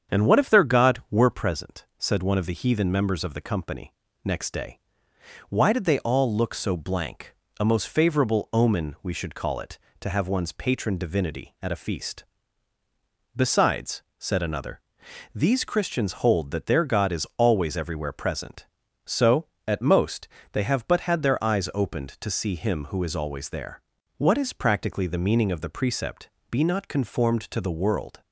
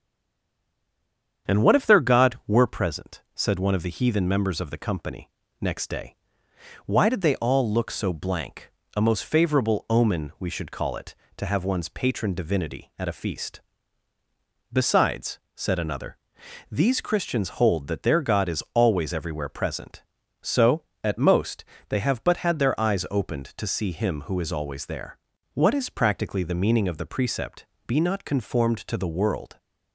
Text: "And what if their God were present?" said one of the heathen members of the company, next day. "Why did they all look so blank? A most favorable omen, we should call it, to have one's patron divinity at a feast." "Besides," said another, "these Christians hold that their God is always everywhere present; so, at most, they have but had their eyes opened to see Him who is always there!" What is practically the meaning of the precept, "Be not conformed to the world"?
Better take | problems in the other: first | stays silent before the first word; noticeable; until 1.4 s; 1.4 s long // starts louder than the rest; strong; until 2.5 s; 8 dB; strong in the first

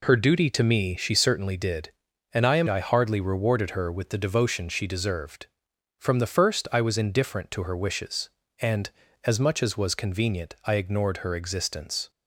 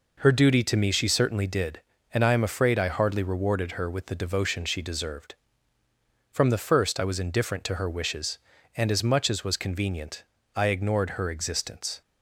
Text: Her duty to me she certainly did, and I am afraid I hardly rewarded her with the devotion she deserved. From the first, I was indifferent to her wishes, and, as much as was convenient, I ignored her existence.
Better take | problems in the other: second | skips "afraid"; at 2.6 s

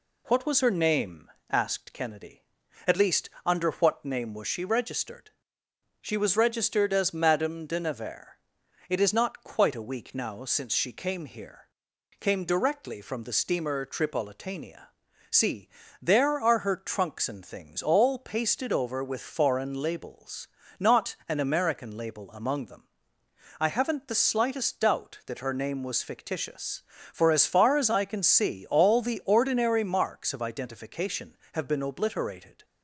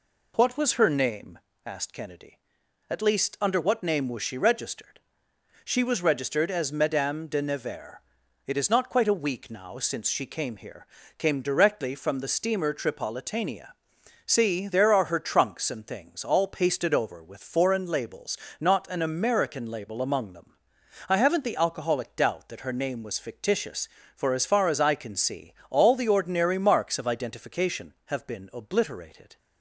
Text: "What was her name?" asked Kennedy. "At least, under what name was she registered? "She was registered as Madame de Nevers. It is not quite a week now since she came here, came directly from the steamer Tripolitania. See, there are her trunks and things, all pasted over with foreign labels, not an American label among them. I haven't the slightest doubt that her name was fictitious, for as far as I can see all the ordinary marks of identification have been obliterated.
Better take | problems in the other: first | says "alcoholic" for "slightest"; at 21.5 s // pauses between "see" and "all"; slight; at 25.5 s; 0.16 s long

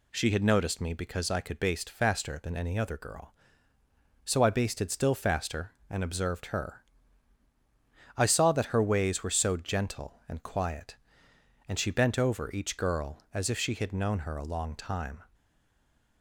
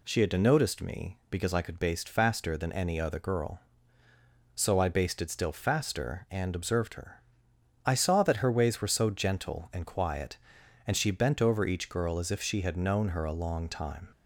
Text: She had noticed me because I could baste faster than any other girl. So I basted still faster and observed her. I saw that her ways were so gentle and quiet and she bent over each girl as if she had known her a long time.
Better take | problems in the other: second | stays silent after the last word; slight; from 15.3 s on; 0.9 s long

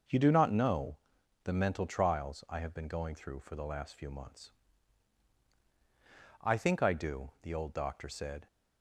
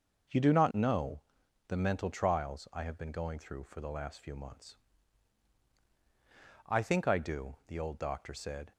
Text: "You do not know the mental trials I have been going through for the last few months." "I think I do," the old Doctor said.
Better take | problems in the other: neither | starts louder than the rest; noticeable; the same in both // pauses between "know" and "the"; noticeable; the same in both

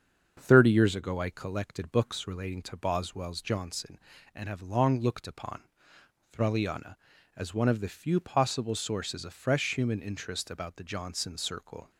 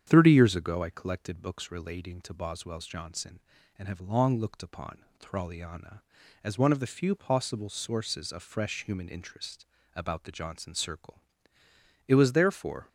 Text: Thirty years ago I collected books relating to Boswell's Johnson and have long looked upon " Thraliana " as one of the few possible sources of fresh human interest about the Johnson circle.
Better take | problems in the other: first | starts louder than the rest; strong; until 1.0 s; 8.5 dB; strong in the first // pauses between "interest" and "about"; slight; at 9.6 s; 0.28 s long // goes on to say "It was therefore"; noticeable; from 12.0 s on; 0.82 s long

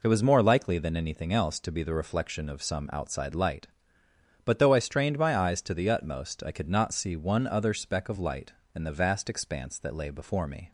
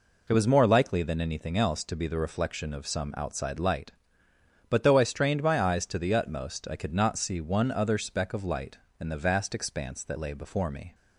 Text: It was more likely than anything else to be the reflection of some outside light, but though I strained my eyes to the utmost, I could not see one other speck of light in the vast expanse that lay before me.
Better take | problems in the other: neither | none

